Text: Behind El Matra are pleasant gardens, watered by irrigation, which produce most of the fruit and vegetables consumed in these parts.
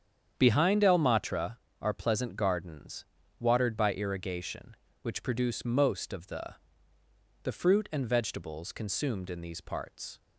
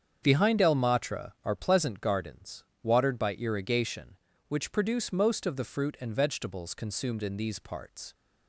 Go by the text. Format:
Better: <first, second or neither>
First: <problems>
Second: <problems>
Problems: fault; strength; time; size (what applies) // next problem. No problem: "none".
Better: second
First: starts louder than the rest; strong; until 1.3 s; 8 dB // says "the" twice; at 7.4 s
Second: starts louder than the rest; strong; until 1.2 s; 7.5 dB